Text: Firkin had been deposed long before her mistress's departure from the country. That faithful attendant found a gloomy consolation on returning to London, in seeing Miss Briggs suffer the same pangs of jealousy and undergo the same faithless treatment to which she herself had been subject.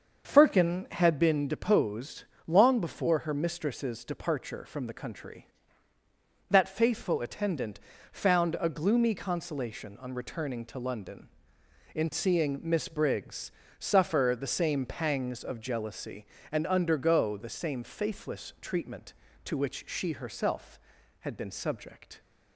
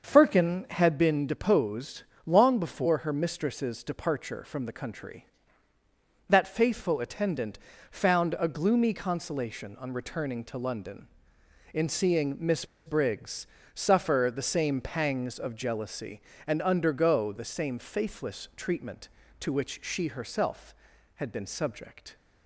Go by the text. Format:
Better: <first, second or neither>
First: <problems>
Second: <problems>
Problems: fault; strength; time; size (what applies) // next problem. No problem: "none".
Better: first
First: starts louder than the rest; until 1.3 s; 6.5 dB // pauses between "deposed" and "long"; slight; at 2.2 s; 0.24 s long // pauses between "attendant" and "found"; slight; at 7.7 s; 0.34 s long // pauses between "Briggs" and "suffer"; slight; at 13.5 s; 0.28 s long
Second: starts louder than the rest; until 1.0 s; 6.5 dB // pauses between "deposed" and "long"; slight; at 2.0 s; 0.24 s long // pauses between "attendant" and "found"; slight; at 7.5 s; 0.34 s long // pauses between "Miss" and "Briggs"; slight; at 12.6 s; 0.20 s long // pauses between "Briggs" and "suffer"; slight; at 13.4 s; 0.28 s long